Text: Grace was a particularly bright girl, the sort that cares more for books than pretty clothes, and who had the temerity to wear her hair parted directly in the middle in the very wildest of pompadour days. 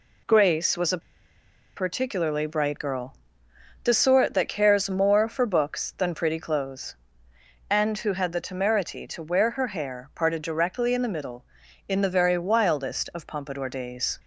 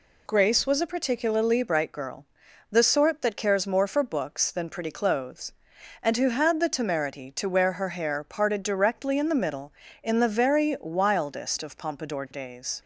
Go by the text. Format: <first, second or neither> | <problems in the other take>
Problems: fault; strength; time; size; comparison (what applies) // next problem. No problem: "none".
second | pauses between "a" and "particularly"; noticeable; at 1.0 s; 0.77 s long